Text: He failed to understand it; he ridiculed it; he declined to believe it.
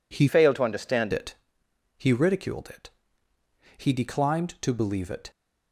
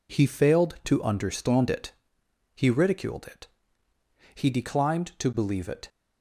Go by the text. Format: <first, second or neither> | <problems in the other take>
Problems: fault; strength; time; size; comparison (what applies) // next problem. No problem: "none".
second | changes voice from "failed" to "understand"; from 0.2 to 1.1 s; 0.9 s long